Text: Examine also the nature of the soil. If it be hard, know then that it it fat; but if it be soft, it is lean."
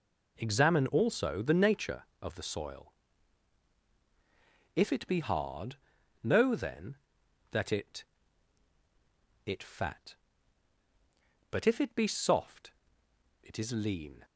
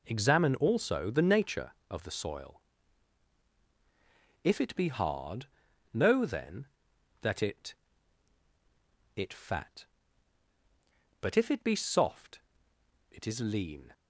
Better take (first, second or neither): neither